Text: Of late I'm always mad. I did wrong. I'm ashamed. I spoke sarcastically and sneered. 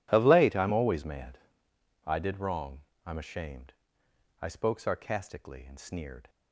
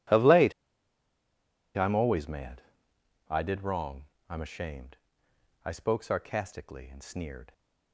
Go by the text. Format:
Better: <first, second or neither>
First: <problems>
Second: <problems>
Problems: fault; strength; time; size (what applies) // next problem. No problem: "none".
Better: first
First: none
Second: pauses between "late" and "I'm"; at 0.5 s; 1.2 s long